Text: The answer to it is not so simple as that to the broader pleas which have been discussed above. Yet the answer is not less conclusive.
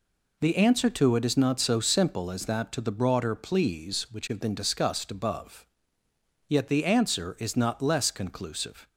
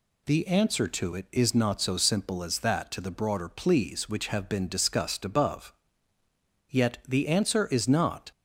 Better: first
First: none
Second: stops before "less conclusive"; at 8.3 s

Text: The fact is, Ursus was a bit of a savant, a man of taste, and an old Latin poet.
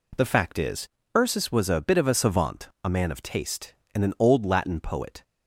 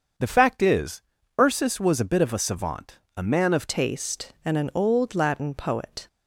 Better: first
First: none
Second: starts louder than the rest; until 1.5 s; 7 dB // changes voice at "taste"; from 3.6 s on; 2.4 s long

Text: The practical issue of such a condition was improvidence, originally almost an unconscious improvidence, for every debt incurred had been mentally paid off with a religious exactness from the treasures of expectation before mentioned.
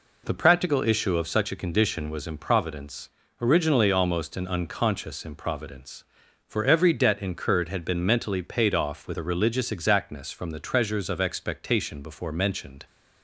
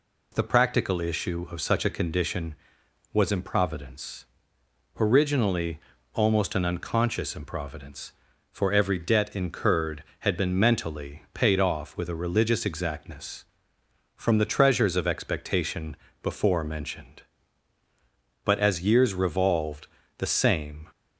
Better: first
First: none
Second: pauses between "originally" and "almost"; slight; at 5.7 s; 0.36 s long // pauses between "expectation" and "before"; slight; at 15.9 s; 0.26 s long // goes on to say "But as years revolved the same"; strong; from 18.4 s on; 2.4 s long

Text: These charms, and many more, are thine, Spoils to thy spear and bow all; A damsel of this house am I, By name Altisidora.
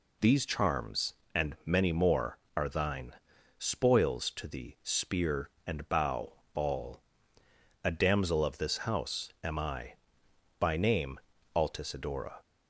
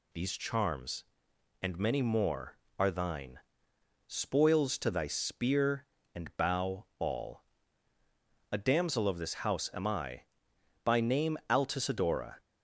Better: second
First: says "thee" for "thy"; at 4.4 s // pauses between "bow" and "all"; slight; at 6.3 s; 0.22 s long // pauses between "name" and "Altisidora"; slight; at 11.1 s; 0.36 s long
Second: none

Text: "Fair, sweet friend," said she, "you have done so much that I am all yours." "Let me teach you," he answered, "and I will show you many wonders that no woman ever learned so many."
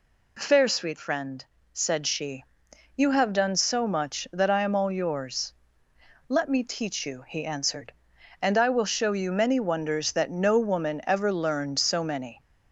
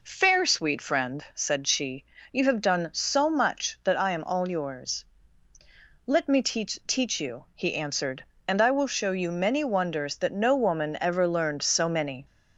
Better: first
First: none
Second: says "teach" twice; at 6.8 s

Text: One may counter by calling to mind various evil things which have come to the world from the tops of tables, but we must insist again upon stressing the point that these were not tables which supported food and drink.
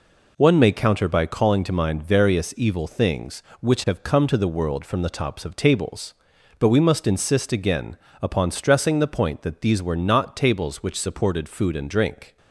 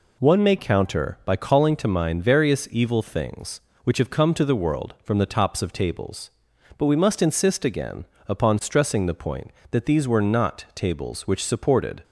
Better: first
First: pauses between "again" and "upon"; slight; at 7.9 s; 0.24 s long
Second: pauses between "again" and "upon"; slight; at 8.0 s; 0.24 s long // stops before "food and drink"; at 12.0 s

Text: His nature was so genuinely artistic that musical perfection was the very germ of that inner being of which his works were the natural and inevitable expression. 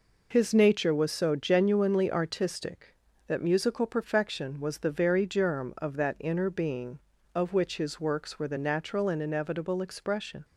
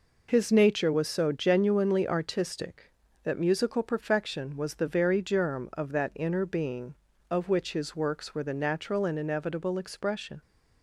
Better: neither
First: none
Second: none

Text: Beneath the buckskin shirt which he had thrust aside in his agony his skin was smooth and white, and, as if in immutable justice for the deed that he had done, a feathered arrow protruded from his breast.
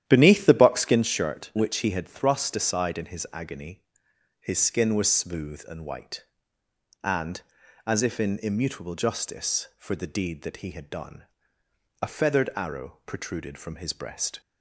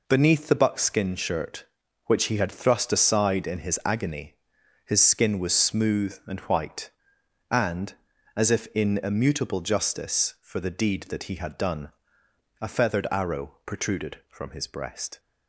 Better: second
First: starts louder than the rest; strong; until 1.0 s; 11 dB // pauses between "agony" and "his"; noticeable; at 3.8 s; 0.56 s long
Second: pauses between "agony" and "his"; noticeable; at 4.3 s; 0.50 s long

